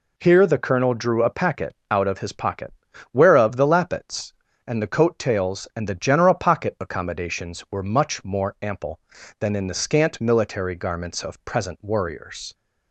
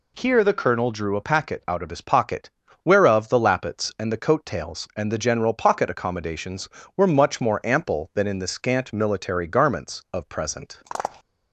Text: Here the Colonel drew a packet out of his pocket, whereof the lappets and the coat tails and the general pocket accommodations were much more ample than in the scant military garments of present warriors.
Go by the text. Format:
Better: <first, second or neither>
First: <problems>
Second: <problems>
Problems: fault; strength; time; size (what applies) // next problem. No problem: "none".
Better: first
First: none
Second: stops before "warriors"; at 11.2 s